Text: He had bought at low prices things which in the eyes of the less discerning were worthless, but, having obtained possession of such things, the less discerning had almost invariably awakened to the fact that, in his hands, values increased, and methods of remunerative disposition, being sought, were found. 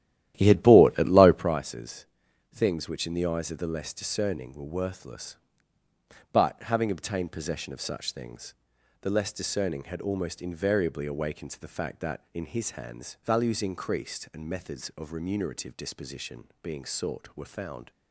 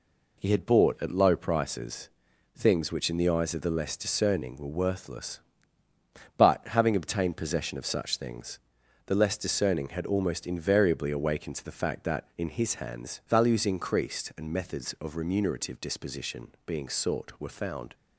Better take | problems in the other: second | starts louder than the rest; strong; until 1.6 s; 12.5 dB // pauses between "prices" and "things"; noticeable; at 2.0 s; 0.46 s long; noticeable in the second

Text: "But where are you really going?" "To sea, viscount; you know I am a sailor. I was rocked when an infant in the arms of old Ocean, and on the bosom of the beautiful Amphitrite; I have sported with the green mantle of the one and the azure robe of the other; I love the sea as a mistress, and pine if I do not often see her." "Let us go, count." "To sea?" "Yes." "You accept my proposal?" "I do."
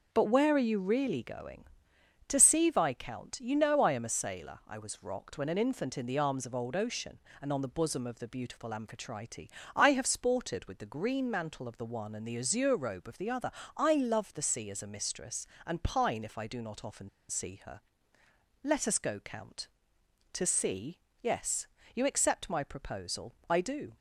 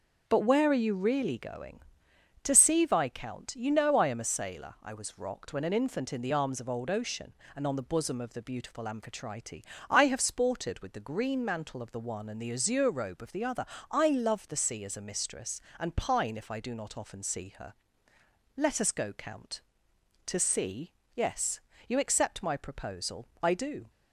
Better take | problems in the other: second | pauses between "often" and "see"; slight; at 17.0 s; 0.20 s long

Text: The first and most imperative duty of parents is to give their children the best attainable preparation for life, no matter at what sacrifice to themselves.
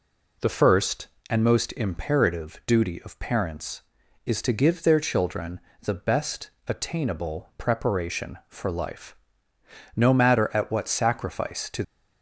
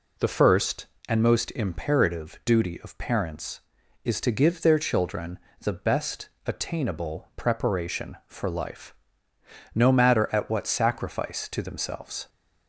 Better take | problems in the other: second | pauses between "children" and "the"; slight; at 5.5 s; 0.24 s long; slight in the second // pauses between "best" and "attainable"; slight; at 6.4 s; 0.18 s long; slight in the second // stops before "themselves"; at 11.8 s

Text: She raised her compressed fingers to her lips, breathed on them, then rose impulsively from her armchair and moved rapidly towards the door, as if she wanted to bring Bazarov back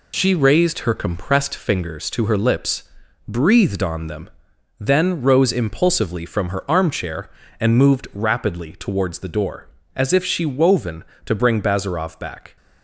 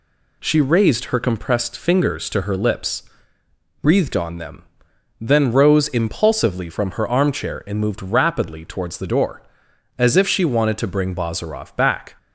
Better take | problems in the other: second | says "woven" for "wanted"; at 10.4 s

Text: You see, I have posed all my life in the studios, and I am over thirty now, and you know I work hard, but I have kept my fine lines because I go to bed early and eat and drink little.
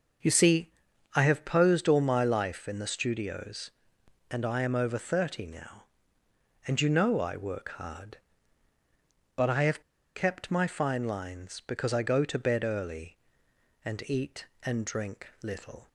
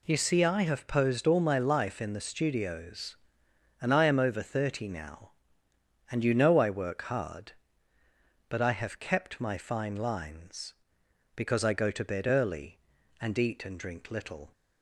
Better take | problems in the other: second | starts louder than the rest; until 1.6 s; 6.5 dB // pauses between "have" and "kept"; slight; at 9.8 s; 0.34 s long // pauses between "drink" and "little"; slight; at 15.2 s; 0.16 s long

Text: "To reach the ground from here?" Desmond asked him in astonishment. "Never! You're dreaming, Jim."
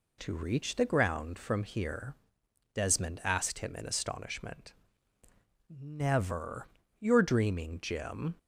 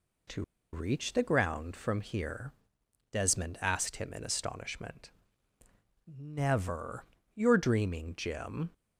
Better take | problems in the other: first | pauses between "To" and "reach"; slight; at 0.4 s; 0.30 s long

